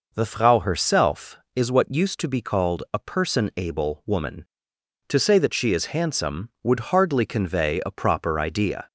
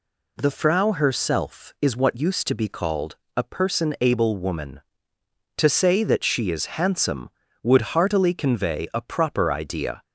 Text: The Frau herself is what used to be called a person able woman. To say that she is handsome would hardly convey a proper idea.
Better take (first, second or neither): first